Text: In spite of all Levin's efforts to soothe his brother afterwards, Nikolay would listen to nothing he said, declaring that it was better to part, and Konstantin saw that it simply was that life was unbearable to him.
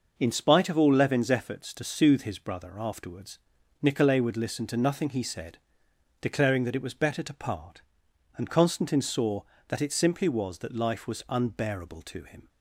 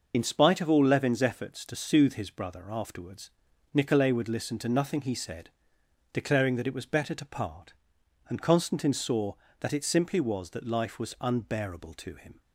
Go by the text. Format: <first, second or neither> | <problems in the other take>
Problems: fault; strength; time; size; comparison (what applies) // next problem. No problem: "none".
first | loses the start of "In"; at 0.1 s; 50 ms